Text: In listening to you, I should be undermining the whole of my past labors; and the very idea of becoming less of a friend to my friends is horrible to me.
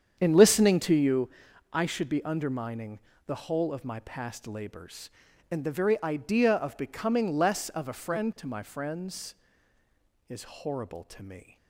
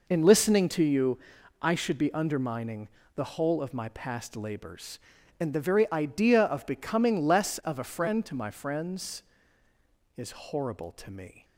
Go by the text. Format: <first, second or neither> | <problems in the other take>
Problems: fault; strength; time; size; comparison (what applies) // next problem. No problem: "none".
second | starts louder than the rest; strong; until 1.3 s; 8 dB // pauses between "undermining" and "the"; slight; at 2.9 s; 0.30 s long; slight in the second